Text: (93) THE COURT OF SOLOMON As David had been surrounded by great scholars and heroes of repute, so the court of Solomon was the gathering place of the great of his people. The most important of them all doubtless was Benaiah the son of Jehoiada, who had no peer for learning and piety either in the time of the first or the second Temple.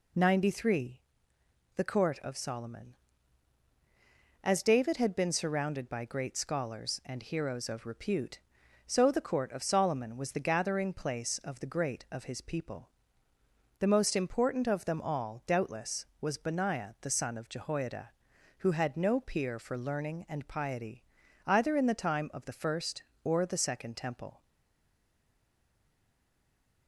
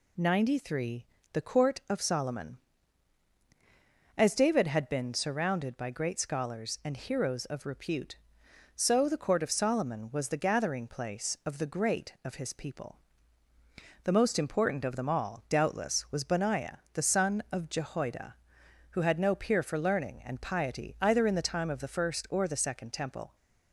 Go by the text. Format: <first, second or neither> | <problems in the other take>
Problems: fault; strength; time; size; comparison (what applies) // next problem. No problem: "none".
second | pauses between "piety" and "either"; at 21.0 s; 0.44 s long // stays silent after the last word; from 24.4 s on; 2.4 s long